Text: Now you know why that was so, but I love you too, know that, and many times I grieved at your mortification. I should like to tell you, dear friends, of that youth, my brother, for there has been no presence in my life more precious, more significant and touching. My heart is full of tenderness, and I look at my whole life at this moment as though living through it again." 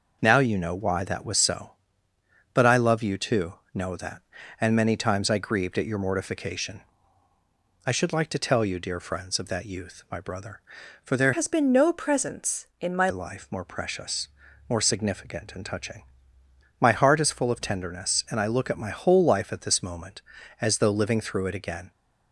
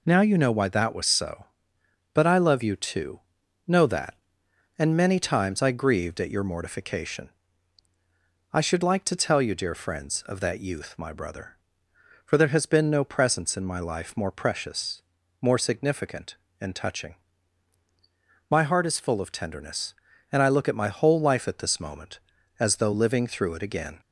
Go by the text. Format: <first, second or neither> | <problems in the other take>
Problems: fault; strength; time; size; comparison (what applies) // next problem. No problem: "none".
second | changes voice from "has" to "my"; from 11.3 to 13.0 s; 1.7 s long